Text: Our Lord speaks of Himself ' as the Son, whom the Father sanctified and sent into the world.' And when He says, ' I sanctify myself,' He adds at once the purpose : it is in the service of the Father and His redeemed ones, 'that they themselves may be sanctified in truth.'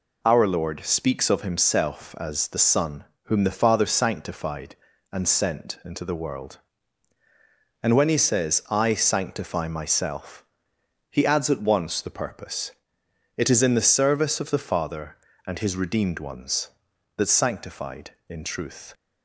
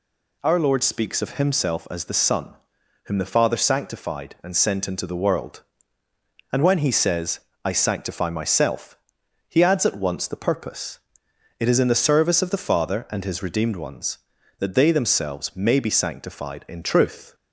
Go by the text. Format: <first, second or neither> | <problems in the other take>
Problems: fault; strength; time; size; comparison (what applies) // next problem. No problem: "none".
second | skips "they themselves may be"; at 17.2 s